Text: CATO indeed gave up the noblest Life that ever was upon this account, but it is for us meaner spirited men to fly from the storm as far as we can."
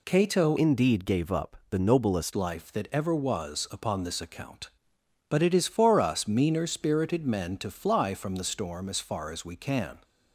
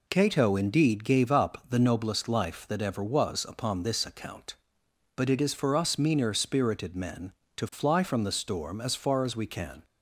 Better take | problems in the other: second | changes voice from "indeed" to "noblest"; from 0.5 to 2.3 s; 1.8 s long

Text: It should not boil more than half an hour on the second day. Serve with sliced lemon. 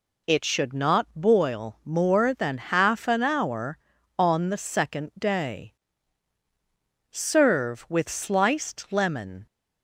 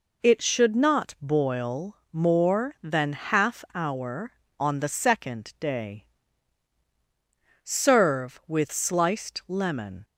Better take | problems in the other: first | pauses between "boil" and "more"; slight; at 1.9 s; 0.16 s long // skips "an"; at 3.6 s

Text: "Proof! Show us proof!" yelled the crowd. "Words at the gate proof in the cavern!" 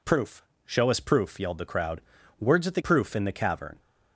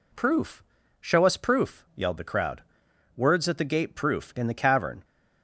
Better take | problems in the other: second | skips "gate"; at 2.8 s

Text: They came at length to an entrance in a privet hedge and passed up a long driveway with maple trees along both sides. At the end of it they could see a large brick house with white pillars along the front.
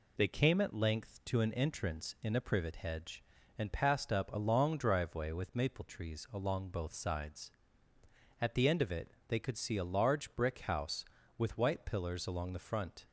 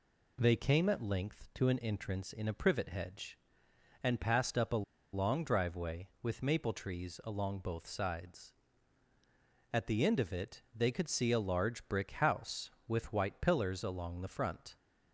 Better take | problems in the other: first | pauses between "a" and "long"; slight; at 4.8 s; 0.31 s long // pauses between "it" and "they"; slight; at 10.6 s; 0.16 s long; slight in the first

